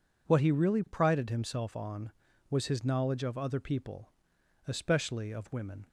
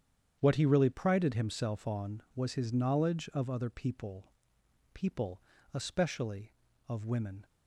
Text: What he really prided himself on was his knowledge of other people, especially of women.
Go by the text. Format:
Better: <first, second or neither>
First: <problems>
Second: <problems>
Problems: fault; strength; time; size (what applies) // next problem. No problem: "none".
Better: first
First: none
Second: starts louder than the rest; strong; until 1.4 s; 8.5 dB // says "people" twice; at 4.9 s